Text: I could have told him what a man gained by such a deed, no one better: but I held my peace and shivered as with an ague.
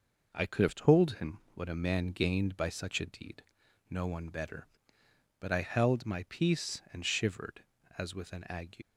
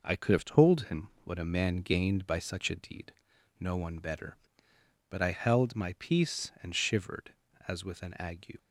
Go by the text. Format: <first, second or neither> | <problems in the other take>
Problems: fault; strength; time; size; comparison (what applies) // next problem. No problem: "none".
second | leaves "ague" unfinished; at 8.8 s; 55 ms